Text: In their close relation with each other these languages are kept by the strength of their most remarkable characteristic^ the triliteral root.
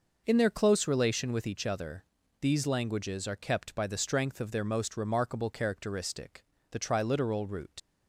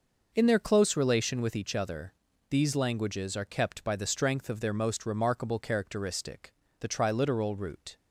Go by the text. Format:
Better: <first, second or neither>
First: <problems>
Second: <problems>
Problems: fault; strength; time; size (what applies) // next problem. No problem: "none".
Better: second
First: pauses between "other" and "these"; slight; at 2.0 s; 0.34 s long // pauses between "characteristic" and "the"; slight; at 6.4 s; 0.24 s long // leaves "root" unfinished; at 7.7 s; 75 ms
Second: pauses between "other" and "these"; slight; at 2.1 s; 0.34 s long // pauses between "characteristic" and "the"; slight; at 6.5 s; 0.24 s long